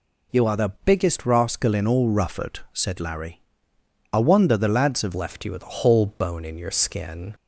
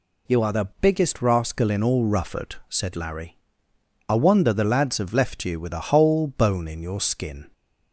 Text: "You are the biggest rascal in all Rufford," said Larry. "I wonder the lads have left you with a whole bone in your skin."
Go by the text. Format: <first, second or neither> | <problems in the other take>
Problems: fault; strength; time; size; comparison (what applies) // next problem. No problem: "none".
second | changes voice at "left"; from 5.1 s on; 2.2 s long